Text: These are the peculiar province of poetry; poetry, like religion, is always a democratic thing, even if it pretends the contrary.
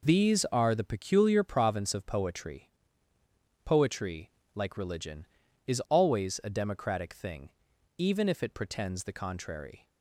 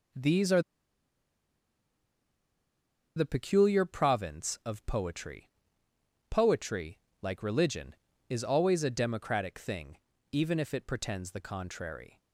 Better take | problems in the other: first | pauses between "are" and "the"; strong; at 0.6 s; 2.5 s long

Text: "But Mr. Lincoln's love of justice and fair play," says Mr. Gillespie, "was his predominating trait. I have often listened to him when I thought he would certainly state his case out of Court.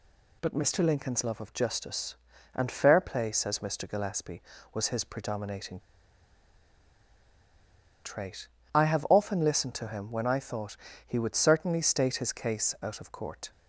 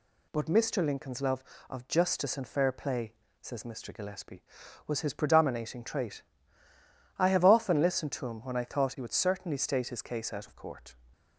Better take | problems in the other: second | pauses between "predominating" and "trait"; strong; at 5.7 s; 2.2 s long // pauses between "thought" and "he"; slight; at 10.7 s; 0.28 s long

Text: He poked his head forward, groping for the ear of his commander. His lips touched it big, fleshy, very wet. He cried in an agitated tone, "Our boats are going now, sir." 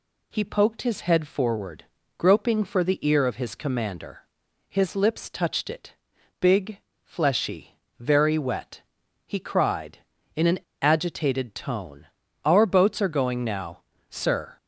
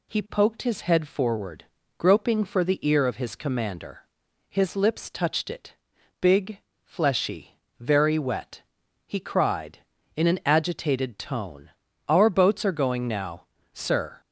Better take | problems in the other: second | pauses between "it" and "big"; noticeable; at 5.9 s; 0.48 s long; noticeable in the second // pauses between "an" and "agitated"; slight; at 10.5 s; 0.23 s long

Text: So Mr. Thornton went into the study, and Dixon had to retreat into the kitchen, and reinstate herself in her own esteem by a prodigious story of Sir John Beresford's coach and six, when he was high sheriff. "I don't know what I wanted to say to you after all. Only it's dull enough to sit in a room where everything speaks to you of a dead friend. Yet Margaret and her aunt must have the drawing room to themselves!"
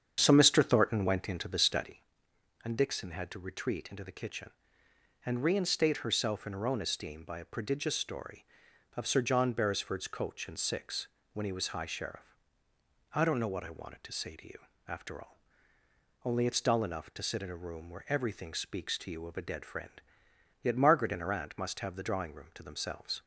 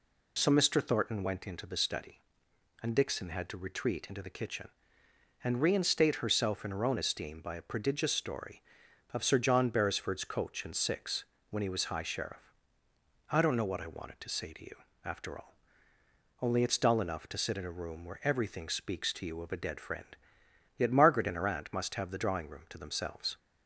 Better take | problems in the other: second | starts louder than the rest; strong; until 2.1 s; 8 dB // pauses between "you" and "after"; slight; at 14.5 s; 0.30 s long; slight in the second

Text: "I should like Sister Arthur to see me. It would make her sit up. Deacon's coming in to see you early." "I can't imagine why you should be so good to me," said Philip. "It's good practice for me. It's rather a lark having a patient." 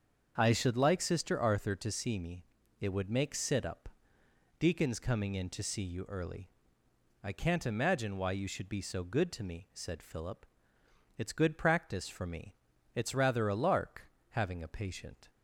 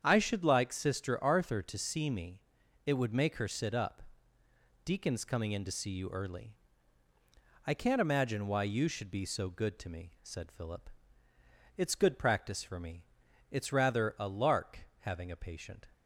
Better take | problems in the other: second | starts louder than the rest; until 1.3 s; 7 dB; strong in the second // skips "her"; at 3.3 s // pauses between "lark" and "having"; slight; at 14.1 s; 0.22 s long; slight in the second

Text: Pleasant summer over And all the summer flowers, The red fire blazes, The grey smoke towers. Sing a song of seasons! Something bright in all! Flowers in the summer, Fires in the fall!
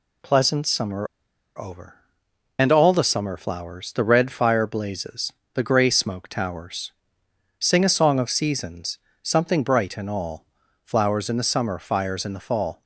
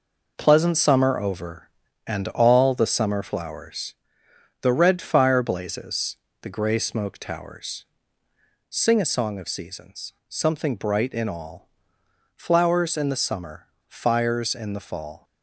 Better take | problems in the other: second | pauses between "summer" and "over"; noticeable; at 1.0 s; 0.53 s long

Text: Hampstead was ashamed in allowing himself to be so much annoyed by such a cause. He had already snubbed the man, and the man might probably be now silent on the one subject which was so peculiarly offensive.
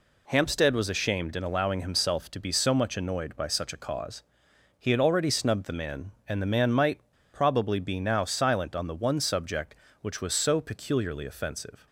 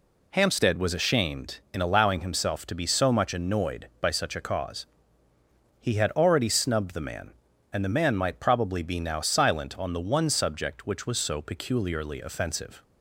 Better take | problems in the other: second | pauses between "might" and "probably"; slight; at 6.9 s; 0.34 s long

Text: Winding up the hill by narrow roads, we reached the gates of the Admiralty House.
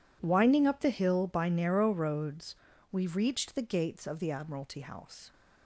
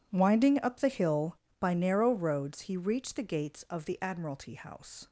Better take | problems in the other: first | says "he" for "we"; at 2.6 s

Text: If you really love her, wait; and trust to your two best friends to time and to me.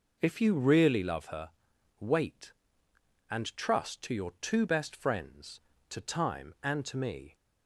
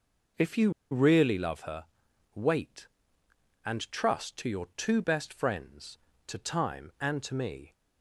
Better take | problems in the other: first | pauses between "you" and "really"; slight; at 0.7 s; 0.20 s long

